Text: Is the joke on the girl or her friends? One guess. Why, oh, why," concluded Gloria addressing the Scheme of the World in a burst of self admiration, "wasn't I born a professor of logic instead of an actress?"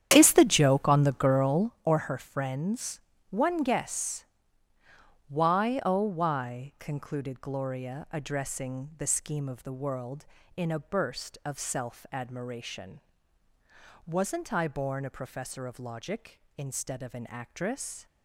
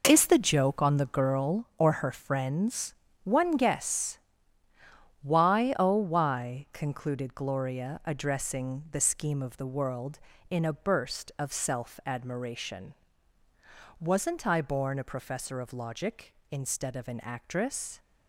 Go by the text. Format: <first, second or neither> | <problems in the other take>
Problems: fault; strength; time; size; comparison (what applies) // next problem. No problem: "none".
second | starts louder than the rest; strong; until 1.9 s; 9.5 dB